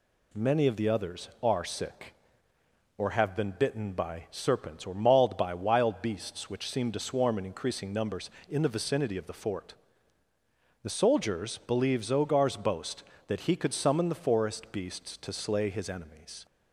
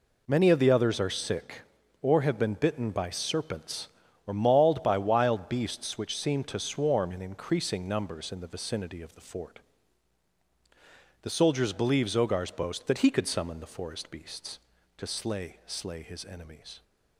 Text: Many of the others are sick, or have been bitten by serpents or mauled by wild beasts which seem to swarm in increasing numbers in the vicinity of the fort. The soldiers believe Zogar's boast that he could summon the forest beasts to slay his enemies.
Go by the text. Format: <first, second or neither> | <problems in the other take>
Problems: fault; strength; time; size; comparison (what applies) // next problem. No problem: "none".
first | says "slay" twice; at 15.6 s